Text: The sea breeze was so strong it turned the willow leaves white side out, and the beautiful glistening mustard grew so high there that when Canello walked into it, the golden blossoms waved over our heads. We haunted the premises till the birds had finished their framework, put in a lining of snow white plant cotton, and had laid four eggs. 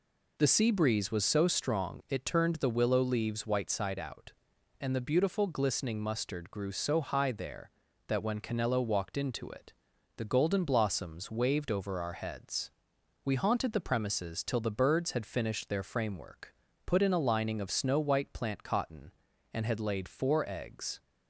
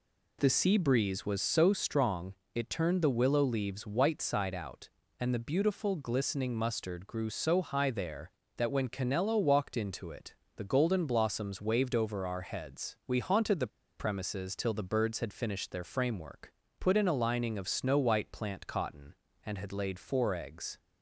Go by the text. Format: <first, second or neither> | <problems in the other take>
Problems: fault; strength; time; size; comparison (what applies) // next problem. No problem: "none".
first | pauses between "strong" and "it"; slight; at 2.3 s; 0.22 s long // pauses between "the" and "premises"; slight; at 13.6 s; 0.30 s long